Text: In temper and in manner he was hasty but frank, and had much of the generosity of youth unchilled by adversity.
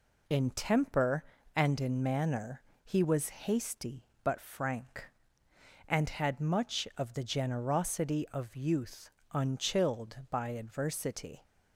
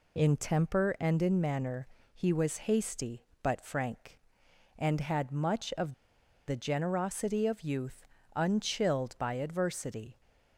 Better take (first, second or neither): first